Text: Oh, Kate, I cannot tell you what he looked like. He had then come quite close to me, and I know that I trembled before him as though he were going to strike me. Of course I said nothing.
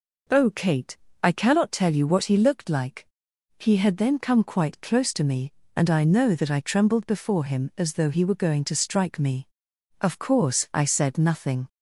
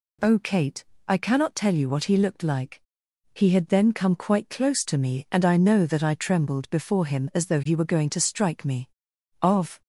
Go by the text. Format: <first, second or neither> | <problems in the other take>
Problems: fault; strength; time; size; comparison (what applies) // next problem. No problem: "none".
first | stops before "course I said nothing"; at 9.8 s